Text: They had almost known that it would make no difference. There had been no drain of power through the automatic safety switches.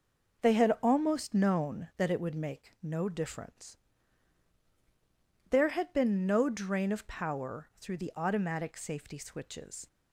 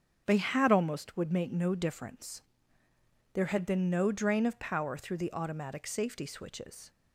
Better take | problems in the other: first | starts louder than the rest; strong; until 1.2 s; 7.5 dB // skips "known that it"; at 1.1 s

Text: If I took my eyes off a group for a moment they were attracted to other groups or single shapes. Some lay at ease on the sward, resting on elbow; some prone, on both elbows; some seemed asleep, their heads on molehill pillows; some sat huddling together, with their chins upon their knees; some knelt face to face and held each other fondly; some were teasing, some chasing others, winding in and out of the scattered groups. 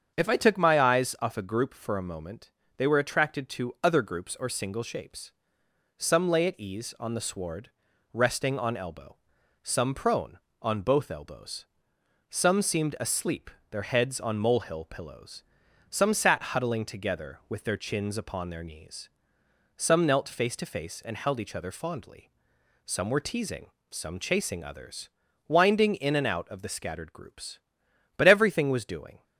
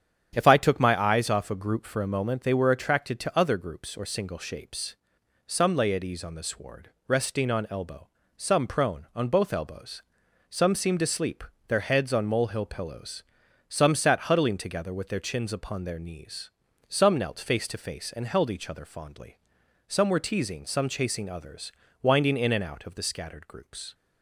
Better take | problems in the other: second | starts louder than the rest; strong; until 1.1 s; 7 dB; strong in the second // pauses between "moment" and "they"; slight; at 2.5 s; 0.26 s long // goes on to say "But everything was doing"; noticeable; from 28.1 s on; 1.0 s long

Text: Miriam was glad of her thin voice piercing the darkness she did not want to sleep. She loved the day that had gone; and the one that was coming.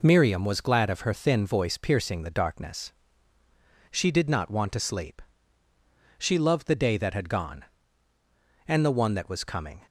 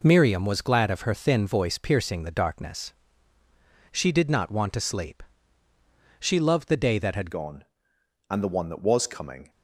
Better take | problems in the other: first | pauses between "darkness" and "she"; at 2.9 s; 1.0 s long; also in the first // changes voice at "gone"; from 7.3 s on; 2.1 s long

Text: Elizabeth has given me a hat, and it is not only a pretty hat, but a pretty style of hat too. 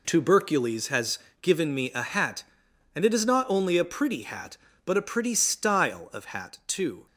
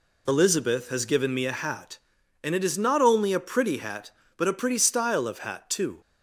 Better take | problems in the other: second | says "Tubercules" for "Elizabeth"; at 0.0 s // pauses between "has" and "given"; slight; at 1.1 s; 0.24 s long

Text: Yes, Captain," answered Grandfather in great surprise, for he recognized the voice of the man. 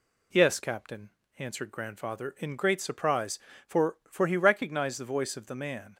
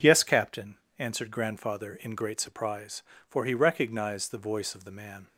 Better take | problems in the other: second | says "for" twice; at 4.0 s

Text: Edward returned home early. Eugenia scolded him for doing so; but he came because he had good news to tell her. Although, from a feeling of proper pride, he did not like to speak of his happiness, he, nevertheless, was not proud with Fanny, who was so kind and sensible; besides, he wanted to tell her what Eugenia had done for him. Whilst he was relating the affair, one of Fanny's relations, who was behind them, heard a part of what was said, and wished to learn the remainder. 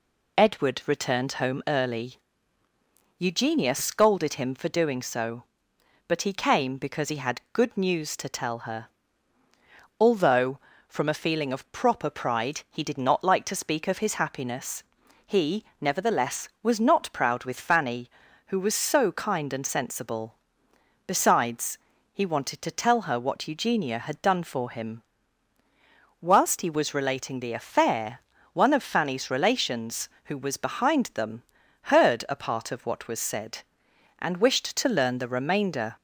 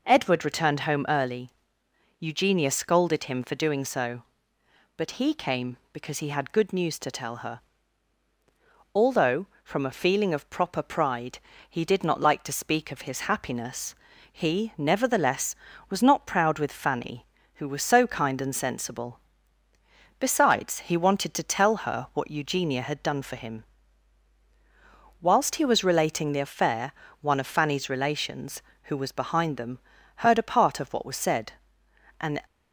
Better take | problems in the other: first | stops before "wished to learn the remainder"; at 32.4 s

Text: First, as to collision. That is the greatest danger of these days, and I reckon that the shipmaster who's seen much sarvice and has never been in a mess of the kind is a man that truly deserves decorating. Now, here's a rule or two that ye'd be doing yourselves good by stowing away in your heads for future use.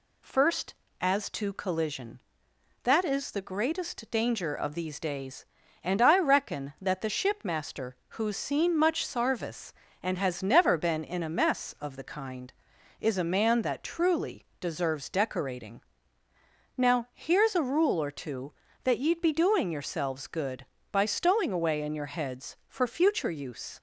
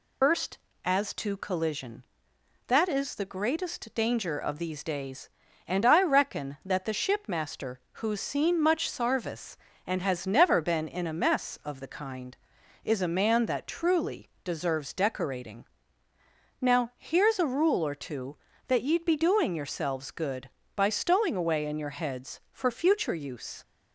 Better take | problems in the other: first | loses the start of "First"; at 0.2 s; 130 ms

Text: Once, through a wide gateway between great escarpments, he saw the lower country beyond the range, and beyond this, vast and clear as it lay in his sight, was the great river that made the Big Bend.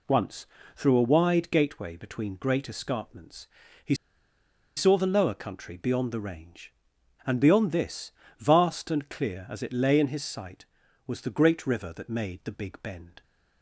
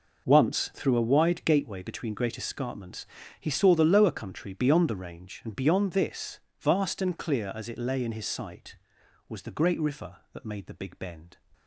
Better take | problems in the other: second | pauses between "he" and "saw"; noticeable; at 3.9 s; 0.82 s long

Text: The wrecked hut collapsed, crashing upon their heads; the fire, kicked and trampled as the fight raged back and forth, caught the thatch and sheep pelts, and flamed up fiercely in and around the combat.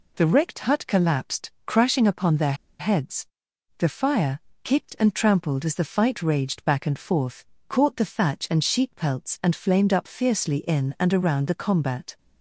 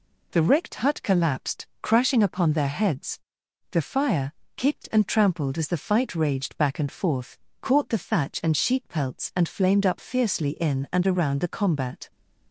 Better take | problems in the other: second | pauses between "their" and "heads"; slight; at 2.5 s; 0.25 s long

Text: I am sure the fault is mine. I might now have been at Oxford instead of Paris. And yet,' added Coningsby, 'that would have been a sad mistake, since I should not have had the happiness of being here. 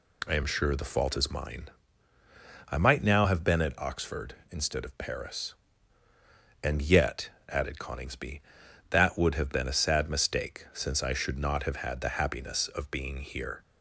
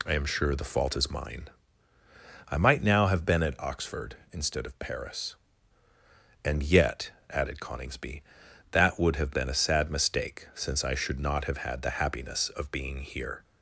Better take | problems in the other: neither | none

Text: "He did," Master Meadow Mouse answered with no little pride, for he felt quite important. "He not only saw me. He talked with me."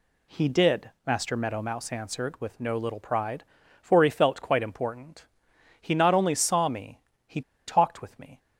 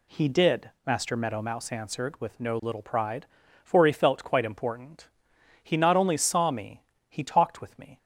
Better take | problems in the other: second | pauses between "He" and "talked"; slight; at 7.4 s; 0.25 s long

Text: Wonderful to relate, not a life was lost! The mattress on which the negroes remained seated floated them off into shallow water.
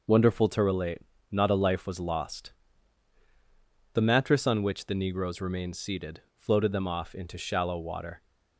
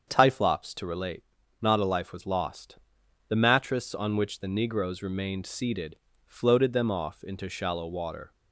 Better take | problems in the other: first | starts louder than the rest; strong; until 1.1 s; 7 dB // says "Typhlops" for "Wonderful"; at 0.0 s // pauses between "seated" and "floated"; slight; at 5.9 s; 0.28 s long; slight in the first

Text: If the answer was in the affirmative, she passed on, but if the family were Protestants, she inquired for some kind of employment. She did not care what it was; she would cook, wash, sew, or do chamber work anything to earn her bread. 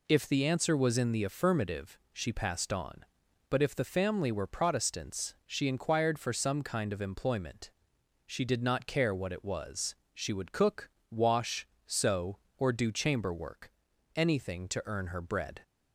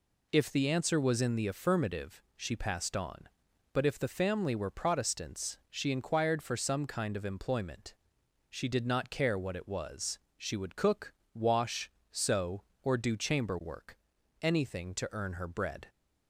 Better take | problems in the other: neither | pauses between "work" and "anything"; the same in both

